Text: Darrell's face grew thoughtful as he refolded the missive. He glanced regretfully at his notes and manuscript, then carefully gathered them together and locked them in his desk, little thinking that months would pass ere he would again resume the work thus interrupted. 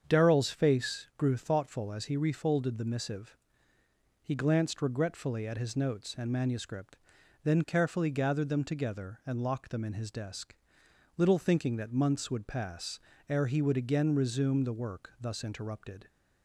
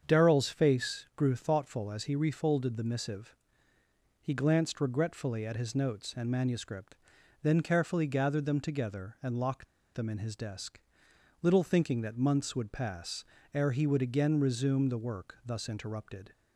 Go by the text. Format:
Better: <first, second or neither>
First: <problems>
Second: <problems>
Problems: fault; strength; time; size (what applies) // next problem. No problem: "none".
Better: first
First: starts louder than the rest; strong; until 1.0 s; 7 dB // pauses between "pass" and "ere"; slight; at 12.9 s; 0.28 s long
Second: starts louder than the rest; strong; until 1.0 s; 7 dB // pauses between "locked" and "them"; slight; at 9.6 s; 0.29 s long // pauses between "pass" and "ere"; slight; at 13.2 s; 0.28 s long